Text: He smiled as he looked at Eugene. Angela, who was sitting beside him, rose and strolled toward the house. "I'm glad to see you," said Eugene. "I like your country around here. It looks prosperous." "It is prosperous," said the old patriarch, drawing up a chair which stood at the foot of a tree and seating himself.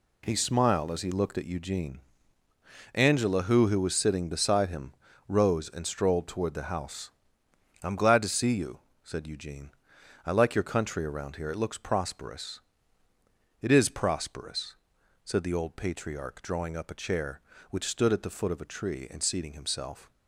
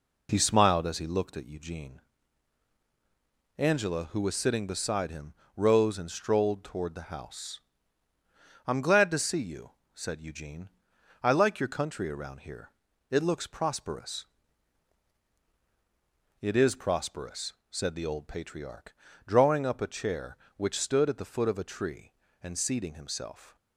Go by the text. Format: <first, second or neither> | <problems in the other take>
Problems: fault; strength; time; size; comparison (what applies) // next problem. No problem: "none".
second | says "who" twice; at 3.6 s